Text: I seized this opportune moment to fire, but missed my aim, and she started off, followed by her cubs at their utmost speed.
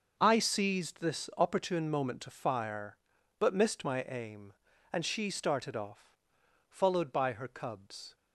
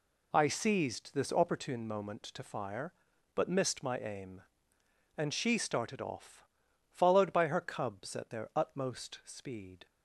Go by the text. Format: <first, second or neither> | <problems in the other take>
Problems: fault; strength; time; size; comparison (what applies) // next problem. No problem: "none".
second | starts louder than the rest; until 1.1 s; 6 dB // stops before "at their utmost speed"; at 8.1 s